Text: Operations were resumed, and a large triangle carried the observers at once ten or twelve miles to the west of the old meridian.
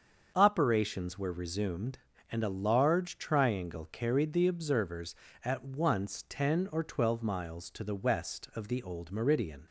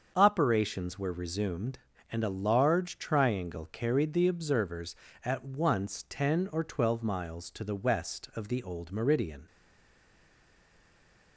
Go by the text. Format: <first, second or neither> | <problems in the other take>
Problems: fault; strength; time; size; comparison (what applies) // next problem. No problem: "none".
first | starts louder than the rest; until 1.1 s; 6.5 dB; also in the first // stays silent after the last word; noticeable; from 9.4 s on; 1.9 s long